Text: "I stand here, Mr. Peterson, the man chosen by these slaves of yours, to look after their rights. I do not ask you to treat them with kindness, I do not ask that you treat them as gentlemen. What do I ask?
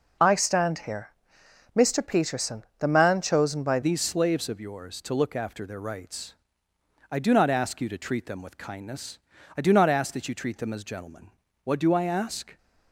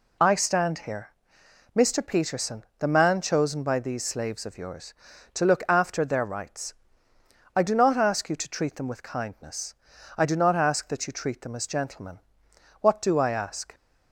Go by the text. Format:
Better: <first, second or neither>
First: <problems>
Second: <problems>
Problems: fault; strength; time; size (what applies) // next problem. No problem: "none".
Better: second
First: changes voice at "these"; from 3.8 s on; 8.7 s long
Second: none